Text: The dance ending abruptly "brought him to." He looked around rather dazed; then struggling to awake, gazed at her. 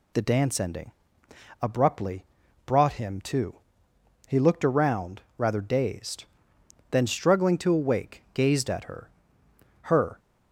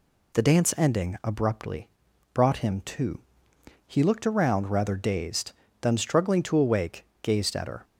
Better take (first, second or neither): second